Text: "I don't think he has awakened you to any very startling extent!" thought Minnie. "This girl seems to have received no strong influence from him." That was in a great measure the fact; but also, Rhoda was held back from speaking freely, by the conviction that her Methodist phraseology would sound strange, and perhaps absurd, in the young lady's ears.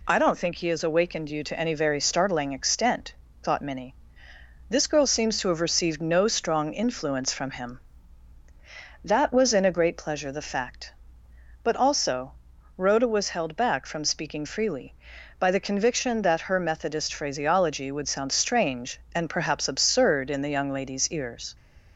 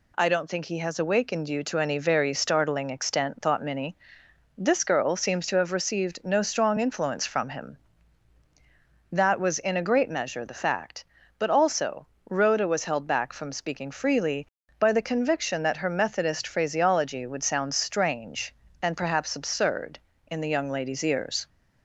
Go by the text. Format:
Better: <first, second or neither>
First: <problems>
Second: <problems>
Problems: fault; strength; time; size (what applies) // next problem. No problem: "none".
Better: second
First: says "pleasure" for "measure"; at 9.9 s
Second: none